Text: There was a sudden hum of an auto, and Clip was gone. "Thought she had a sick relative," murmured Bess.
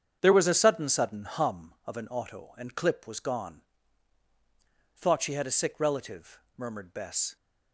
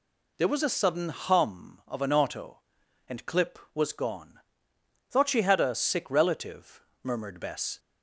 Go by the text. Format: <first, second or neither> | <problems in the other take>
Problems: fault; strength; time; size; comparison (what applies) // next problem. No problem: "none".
second | starts louder than the rest; strong; until 1.2 s; 8 dB // says "sudden" twice; at 0.8 s